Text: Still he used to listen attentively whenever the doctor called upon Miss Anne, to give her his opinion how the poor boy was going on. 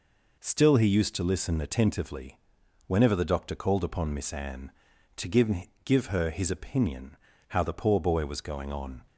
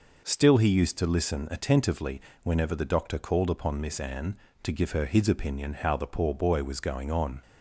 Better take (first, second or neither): second